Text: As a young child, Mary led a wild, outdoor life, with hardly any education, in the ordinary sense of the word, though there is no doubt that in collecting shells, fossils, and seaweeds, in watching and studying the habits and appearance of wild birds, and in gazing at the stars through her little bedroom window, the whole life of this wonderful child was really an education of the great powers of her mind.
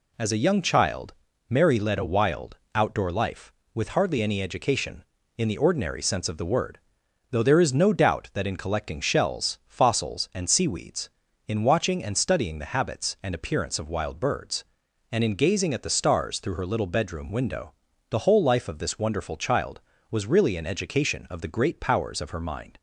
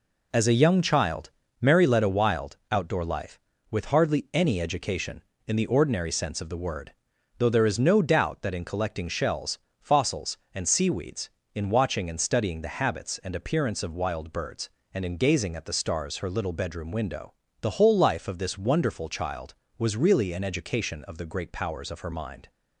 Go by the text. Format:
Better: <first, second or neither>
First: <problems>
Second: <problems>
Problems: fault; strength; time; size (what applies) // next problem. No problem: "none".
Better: first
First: none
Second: skips "through"; at 16.1 s